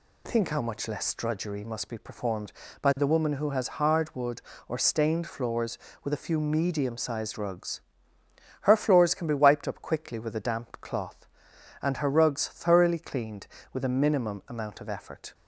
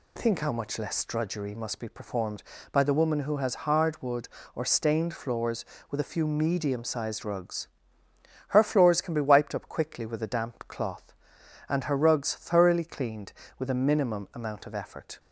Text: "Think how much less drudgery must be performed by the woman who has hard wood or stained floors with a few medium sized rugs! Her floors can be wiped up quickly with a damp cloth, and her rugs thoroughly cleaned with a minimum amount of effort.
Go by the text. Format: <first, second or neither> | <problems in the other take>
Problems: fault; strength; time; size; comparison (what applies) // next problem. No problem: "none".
neither | none